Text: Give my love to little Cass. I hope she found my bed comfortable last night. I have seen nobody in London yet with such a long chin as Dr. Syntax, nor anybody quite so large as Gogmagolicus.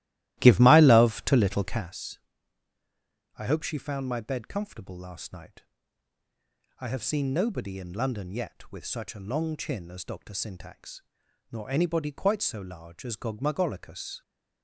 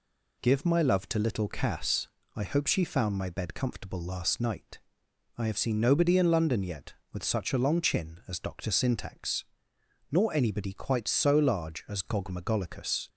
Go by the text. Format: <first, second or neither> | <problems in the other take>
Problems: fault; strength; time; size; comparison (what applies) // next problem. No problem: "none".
second | starts louder than the rest; strong; until 1.9 s; 15.5 dB